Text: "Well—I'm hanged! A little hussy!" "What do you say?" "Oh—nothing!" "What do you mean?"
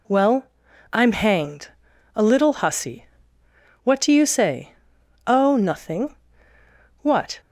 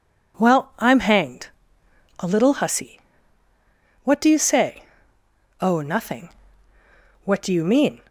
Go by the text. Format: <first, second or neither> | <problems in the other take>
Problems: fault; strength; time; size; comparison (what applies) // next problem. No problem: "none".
second | stops before "do you mean"; at 7.3 s